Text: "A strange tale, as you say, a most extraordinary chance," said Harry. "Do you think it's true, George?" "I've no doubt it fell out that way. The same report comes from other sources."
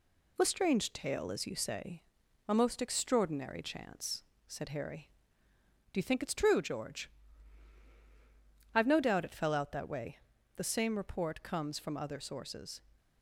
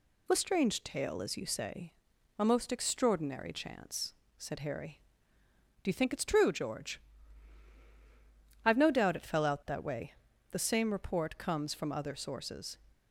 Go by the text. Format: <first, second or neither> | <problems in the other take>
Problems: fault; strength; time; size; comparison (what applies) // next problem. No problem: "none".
second | gets quieter; slight; throughout; 3 dB